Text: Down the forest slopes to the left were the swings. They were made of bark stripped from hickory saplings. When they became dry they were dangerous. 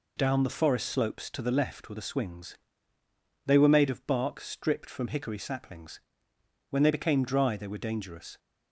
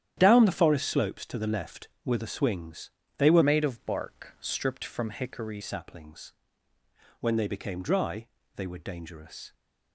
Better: first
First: none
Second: starts louder than the rest; strong; until 1.1 s; 10.5 dB // changes voice from "made" to "hickory"; from 3.4 to 5.6 s; 2.2 s long // pauses between "dry" and "they"; slight; at 8.2 s; 0.30 s long

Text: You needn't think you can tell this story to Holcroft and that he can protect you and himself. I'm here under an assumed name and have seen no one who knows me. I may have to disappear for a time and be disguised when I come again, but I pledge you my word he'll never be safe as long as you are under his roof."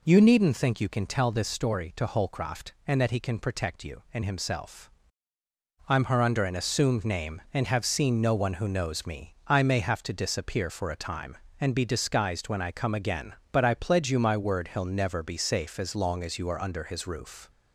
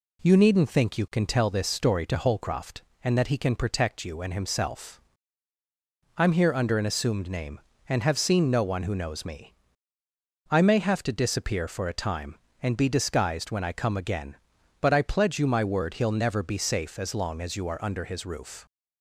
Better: second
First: says "her" for "here"; at 6.0 s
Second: none

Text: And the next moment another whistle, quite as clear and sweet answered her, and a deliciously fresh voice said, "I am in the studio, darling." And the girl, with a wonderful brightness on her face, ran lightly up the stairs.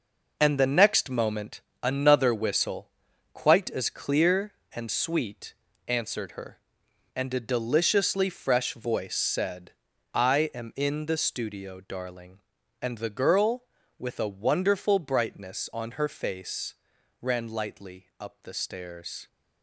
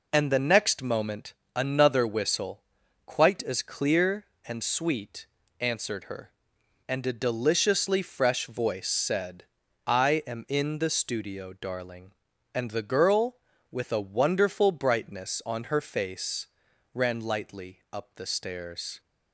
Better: second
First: gets quieter; strong; throughout; 8.5 dB // pauses between "moment" and "another"; slight; at 1.6 s; 0.22 s long // pauses between "sweet" and "answered"; slight; at 5.5 s; 0.34 s long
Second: pauses between "moment" and "another"; slight; at 1.3 s; 0.22 s long // pauses between "sweet" and "answered"; slight; at 5.2 s; 0.34 s long

